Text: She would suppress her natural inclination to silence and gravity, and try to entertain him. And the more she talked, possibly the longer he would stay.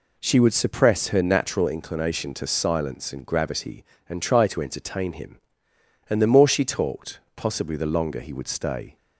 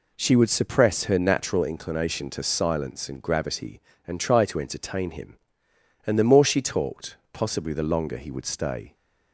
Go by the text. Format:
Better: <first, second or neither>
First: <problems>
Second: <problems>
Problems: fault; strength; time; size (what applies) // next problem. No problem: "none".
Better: neither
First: none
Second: none